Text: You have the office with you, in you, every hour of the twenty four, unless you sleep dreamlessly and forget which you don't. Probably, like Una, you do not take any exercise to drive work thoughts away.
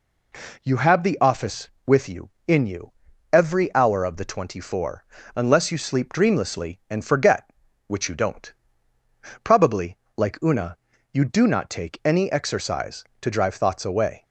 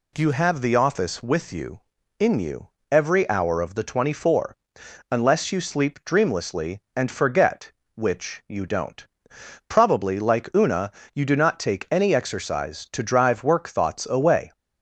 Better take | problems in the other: second | skips "work"; at 13.5 s

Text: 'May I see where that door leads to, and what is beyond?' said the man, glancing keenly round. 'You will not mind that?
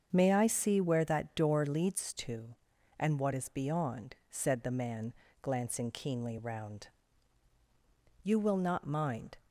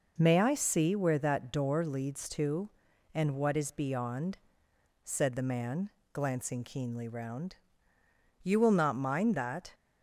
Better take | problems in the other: second | starts louder than the rest; until 1.1 s; 7 dB // stops before "that"; at 9.4 s

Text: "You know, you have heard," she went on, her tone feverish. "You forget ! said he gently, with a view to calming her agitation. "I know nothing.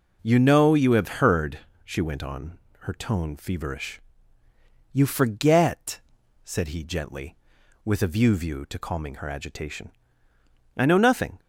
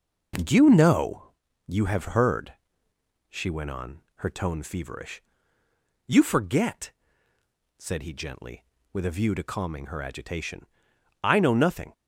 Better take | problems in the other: second | says "view" twice; at 8.3 s

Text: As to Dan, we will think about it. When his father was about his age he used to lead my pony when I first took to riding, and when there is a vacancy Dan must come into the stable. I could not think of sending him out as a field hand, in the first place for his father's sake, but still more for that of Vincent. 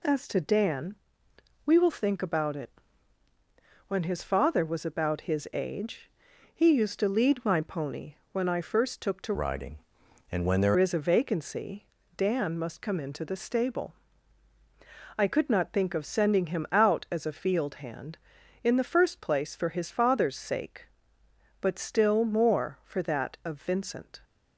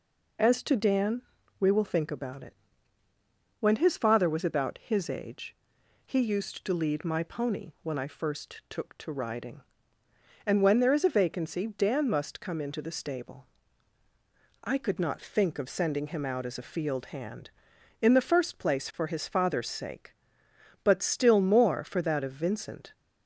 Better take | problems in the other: second | pauses between "age" and "he"; at 6.0 s; 0.44 s long; noticeable in the second // pauses between "pony" and "when"; slight; at 8.1 s; 0.18 s long // changes voice from "riding" to "there"; from 9.3 to 10.7 s; 1.4 s long // pauses between "vacancy" and "Dan"; slight; at 11.8 s; 0.30 s long

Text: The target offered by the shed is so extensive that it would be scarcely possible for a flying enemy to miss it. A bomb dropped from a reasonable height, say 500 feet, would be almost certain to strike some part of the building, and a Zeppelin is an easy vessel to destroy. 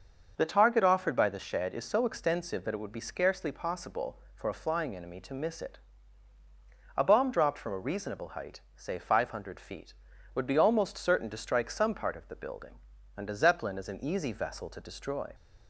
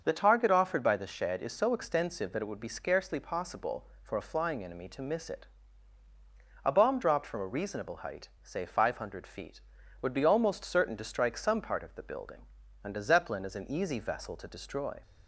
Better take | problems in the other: neither | starts louder than the rest; the same in both

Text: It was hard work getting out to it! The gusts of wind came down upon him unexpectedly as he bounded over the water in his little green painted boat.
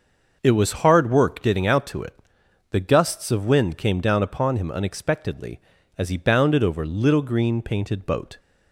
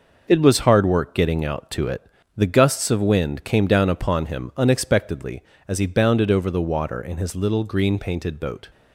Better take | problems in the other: second | starts louder than the rest; noticeable; until 1.4 s; 6 dB // skips "the water in his"; at 6.8 s

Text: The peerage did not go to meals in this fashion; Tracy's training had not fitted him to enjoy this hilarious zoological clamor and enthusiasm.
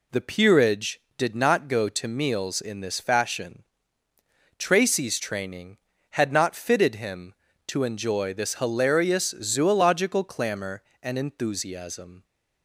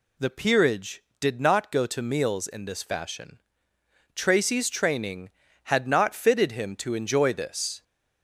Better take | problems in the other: first | stops before "hilarious zoological clamor and enthusiasm"; at 7.8 s

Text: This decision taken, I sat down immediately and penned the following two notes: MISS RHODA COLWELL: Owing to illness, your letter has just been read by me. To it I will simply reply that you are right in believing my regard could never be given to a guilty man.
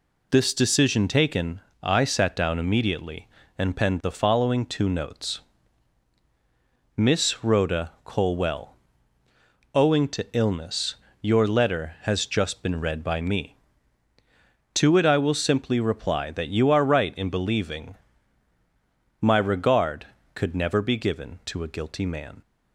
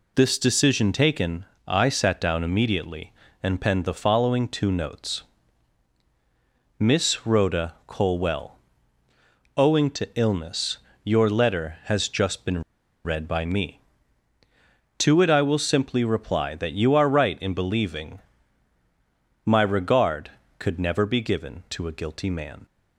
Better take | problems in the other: first | pauses between "RHODA" and "COLWELL"; slight; at 7.7 s; 0.16 s long; slight in the first // pauses between "been" and "read"; at 12.6 s; 0.42 s long // pauses between "believing" and "my"; at 18.2 s; 1.2 s long; also in the first

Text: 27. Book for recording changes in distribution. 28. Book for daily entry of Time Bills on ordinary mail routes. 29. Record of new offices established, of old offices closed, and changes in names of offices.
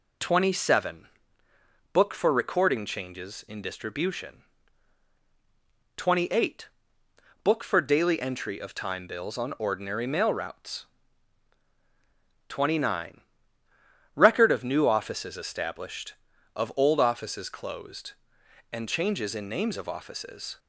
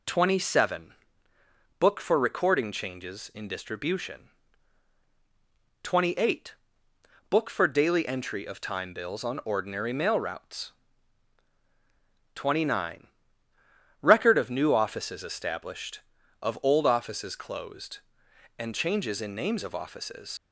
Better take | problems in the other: first | leaves "offices" unfinished; at 20.3 s; 75 ms

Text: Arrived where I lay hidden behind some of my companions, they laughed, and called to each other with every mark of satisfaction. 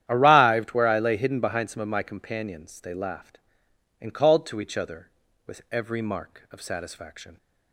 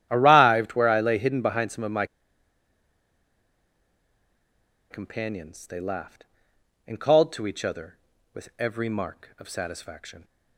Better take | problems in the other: first | starts louder than the rest; strong; until 1.1 s; 11 dB; strong in the first // pauses between "my" and "companions"; strong; at 2.0 s; 2.8 s long

